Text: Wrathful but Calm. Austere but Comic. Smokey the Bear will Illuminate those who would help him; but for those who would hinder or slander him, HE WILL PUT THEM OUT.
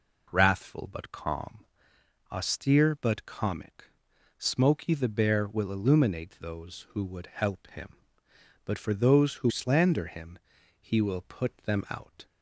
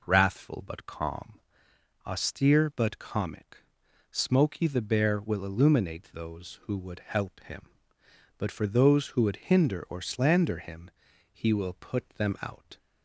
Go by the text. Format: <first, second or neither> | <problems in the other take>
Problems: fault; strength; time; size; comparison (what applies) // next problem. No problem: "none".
second | skips "would hinder or"; at 9.4 s